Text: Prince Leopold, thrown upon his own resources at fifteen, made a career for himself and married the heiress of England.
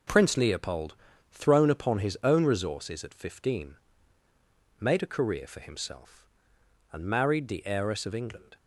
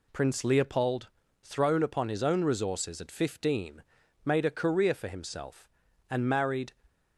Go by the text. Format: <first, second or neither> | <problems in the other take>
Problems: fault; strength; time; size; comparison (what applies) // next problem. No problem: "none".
first | stops before "the heiress of England"; at 6.8 s